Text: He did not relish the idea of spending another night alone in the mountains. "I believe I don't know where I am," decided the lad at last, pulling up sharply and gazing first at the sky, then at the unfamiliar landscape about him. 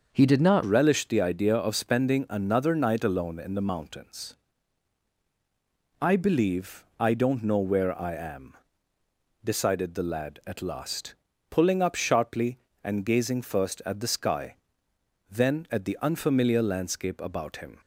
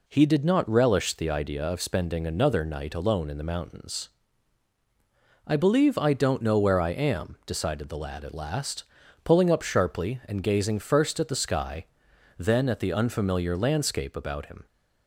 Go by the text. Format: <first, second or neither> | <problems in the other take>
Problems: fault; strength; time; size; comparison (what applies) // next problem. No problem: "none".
second | starts louder than the rest; until 1.1 s; 6.5 dB // changes voice at "relish"; from 0.6 s on; 17.1 s long